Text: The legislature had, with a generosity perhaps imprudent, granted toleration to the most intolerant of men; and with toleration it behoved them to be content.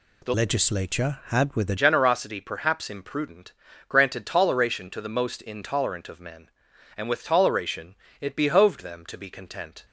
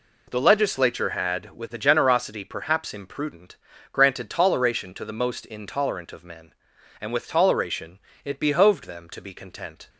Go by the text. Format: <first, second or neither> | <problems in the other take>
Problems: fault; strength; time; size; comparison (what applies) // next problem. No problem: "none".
second | changes voice from "legislature" to "a"; from 0.3 to 1.7 s; 1.4 s long // pauses between "toleration" and "it"; slight; at 7.9 s; 0.24 s long; slight in the second